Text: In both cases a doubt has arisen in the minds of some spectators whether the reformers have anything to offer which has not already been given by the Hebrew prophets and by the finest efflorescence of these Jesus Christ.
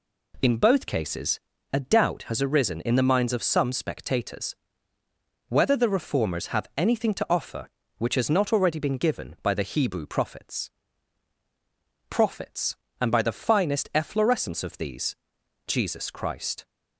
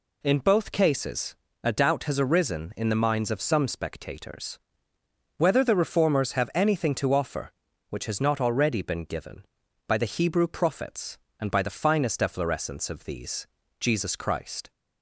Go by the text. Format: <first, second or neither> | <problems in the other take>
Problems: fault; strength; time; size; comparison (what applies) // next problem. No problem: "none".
second | pauses between "cases" and "a"; slight; at 1.3 s; 0.34 s long; slight in the second // pauses between "spectators" and "whether"; noticeable; at 4.5 s; 0.94 s long; noticeable in the second // says "prophets" twice; at 12.0 s // pauses between "these" and "Jesus"; noticeable; at 15.1 s; 0.52 s long; slight in the second